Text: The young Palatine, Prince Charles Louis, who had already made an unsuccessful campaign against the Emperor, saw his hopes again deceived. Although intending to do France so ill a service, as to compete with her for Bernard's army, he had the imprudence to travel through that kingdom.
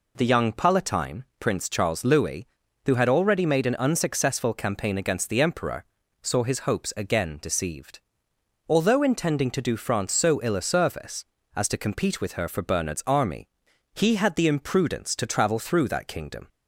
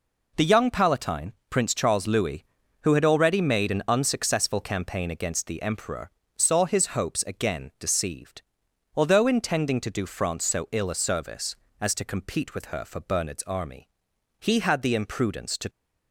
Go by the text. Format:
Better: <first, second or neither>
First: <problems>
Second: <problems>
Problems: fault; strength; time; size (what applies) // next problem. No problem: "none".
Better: first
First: none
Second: stops before "travel through that kingdom"; at 15.6 s